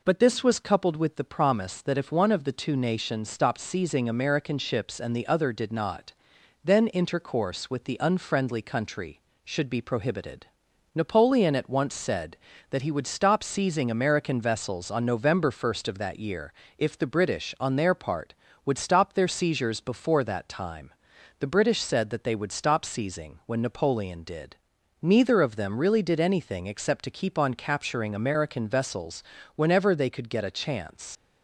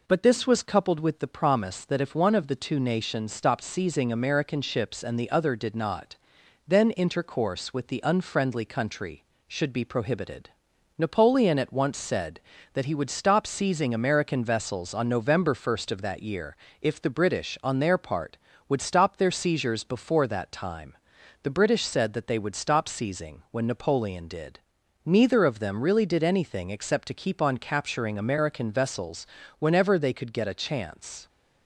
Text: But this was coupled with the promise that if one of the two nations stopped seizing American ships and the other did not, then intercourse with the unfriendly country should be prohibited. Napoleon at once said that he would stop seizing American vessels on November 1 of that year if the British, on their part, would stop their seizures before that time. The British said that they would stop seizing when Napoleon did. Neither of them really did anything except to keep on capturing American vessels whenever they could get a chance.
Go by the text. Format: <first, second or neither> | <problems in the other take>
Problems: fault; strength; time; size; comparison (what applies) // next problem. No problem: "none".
second | pauses between "year" and "if"; slight; at 16.5 s; 0.26 s long; slight in the second // pauses between "vessels" and "whenever"; slight; at 29.2 s; 0.32 s long; slight in the second // leaves "chance" unfinished; at 31.1 s; 95 ms